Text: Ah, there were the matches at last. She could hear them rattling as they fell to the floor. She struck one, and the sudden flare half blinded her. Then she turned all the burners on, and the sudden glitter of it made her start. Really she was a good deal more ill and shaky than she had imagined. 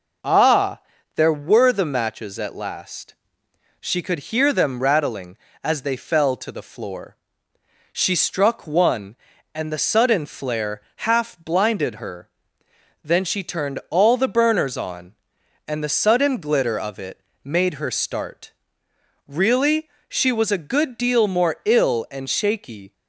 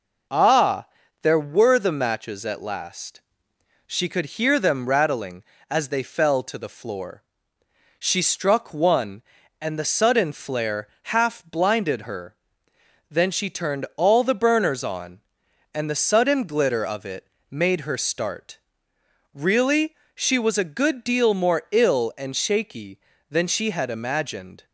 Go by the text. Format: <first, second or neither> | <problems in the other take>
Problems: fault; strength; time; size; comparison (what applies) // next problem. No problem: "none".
second | pauses between "flare" and "half"; slight; at 10.8 s; 0.16 s long; slight in the second // pauses between "it" and "made"; slight; at 17.2 s; 0.24 s long; slight in the second // pauses between "Really" and "she"; slight; at 19.8 s; 0.20 s long; slight in the second // stops before "than she had imagined"; at 22.9 s